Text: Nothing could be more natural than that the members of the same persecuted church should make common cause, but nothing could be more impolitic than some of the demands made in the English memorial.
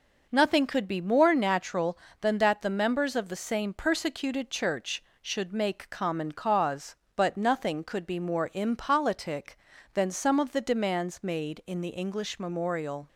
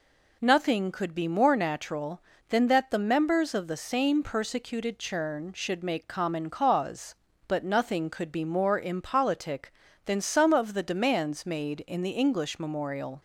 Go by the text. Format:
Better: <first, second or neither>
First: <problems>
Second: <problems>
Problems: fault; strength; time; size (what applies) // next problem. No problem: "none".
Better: first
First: none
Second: says "churn" for "church"; at 4.9 s